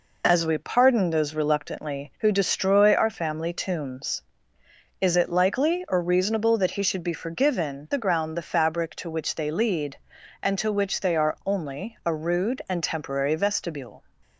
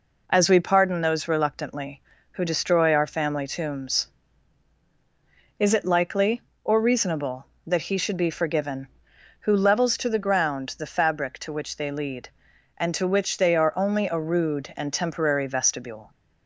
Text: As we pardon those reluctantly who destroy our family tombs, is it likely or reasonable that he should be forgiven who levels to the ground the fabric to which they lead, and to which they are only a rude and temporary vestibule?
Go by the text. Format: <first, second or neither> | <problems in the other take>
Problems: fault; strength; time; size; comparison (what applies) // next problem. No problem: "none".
second | skips "who levels to"; at 7.9 s